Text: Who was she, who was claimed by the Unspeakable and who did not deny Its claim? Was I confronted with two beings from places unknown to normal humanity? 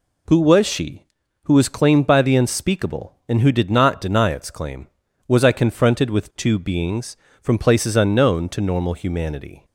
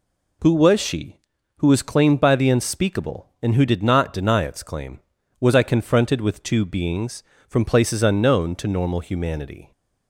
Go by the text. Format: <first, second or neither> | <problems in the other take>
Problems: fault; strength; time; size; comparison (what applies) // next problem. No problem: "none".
neither | none